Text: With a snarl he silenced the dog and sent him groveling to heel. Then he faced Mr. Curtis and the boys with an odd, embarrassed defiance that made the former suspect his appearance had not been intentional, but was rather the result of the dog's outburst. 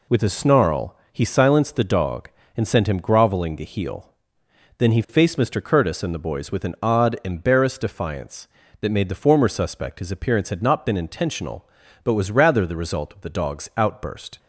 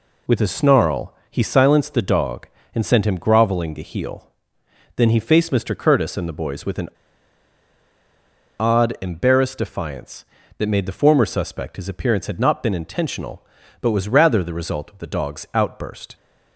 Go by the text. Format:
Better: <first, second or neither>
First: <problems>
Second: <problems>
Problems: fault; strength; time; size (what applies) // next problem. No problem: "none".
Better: first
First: pauses between "snarl" and "he"; slight; at 0.9 s; 0.16 s long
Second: pauses between "snarl" and "he"; slight; at 1.1 s; 0.16 s long // pauses between "an" and "odd"; strong; at 6.8 s; 1.7 s long